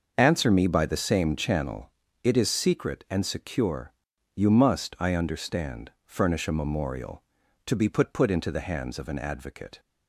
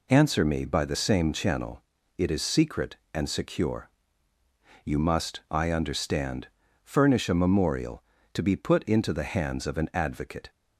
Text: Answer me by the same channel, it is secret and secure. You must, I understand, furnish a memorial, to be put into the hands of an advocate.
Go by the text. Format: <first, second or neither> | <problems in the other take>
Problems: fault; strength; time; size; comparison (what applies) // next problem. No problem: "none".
second | starts louder than the rest; until 1.1 s; 6.5 dB // says "put" twice; at 8.1 s